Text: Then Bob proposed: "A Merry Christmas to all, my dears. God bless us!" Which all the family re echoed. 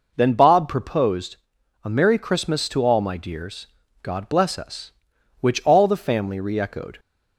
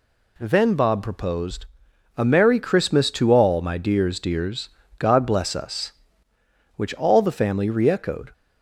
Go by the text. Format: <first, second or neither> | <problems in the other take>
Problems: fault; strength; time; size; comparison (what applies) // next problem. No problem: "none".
first | says "dears" twice; at 4.1 s